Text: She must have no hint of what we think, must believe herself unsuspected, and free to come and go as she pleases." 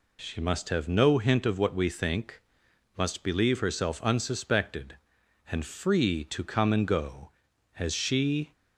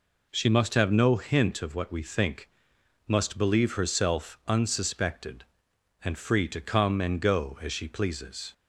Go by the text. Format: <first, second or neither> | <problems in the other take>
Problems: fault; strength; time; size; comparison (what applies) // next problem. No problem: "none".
second | stops before "pleases"; at 8.5 s